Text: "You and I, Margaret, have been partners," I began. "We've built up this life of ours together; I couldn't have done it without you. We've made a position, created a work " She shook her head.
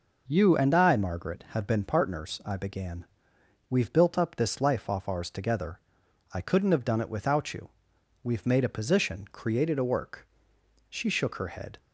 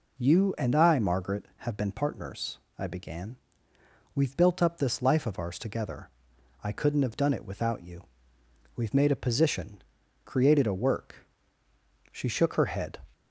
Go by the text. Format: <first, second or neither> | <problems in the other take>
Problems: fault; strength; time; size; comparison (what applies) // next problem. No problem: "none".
second | says "off" for "of"; at 4.8 s